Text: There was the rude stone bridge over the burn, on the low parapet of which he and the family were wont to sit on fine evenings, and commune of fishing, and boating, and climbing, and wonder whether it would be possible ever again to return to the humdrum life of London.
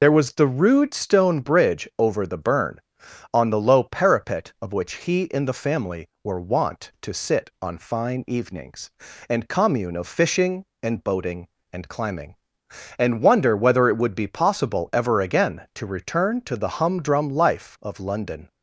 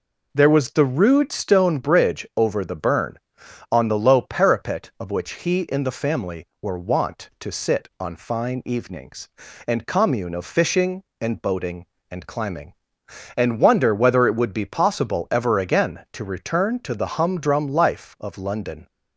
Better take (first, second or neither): second